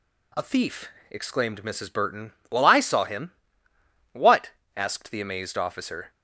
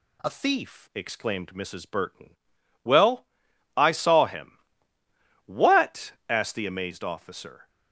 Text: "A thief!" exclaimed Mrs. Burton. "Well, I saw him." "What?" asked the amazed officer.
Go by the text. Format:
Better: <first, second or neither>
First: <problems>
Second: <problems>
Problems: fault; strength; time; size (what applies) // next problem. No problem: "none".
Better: first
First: none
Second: changes voice at "thief"; from 0.2 s on; 7.4 s long